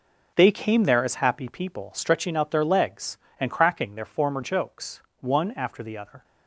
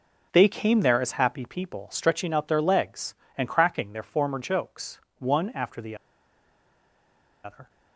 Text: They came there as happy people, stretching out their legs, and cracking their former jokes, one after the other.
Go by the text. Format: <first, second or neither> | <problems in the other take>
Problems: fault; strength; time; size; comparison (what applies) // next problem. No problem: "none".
first | pauses between "the" and "other"; strong; at 5.9 s; 1.4 s long